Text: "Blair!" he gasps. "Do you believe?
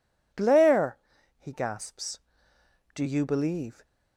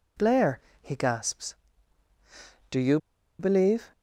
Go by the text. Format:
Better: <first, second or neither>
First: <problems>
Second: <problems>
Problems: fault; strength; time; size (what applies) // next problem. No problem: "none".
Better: first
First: none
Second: pauses between "you" and "believe"; at 2.9 s; 0.41 s long